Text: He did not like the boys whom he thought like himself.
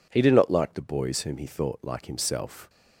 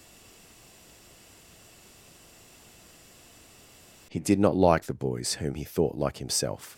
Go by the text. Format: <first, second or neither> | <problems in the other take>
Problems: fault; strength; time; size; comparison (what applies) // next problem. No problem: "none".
first | stays silent before the first word; strong; until 4.1 s; 4.1 s long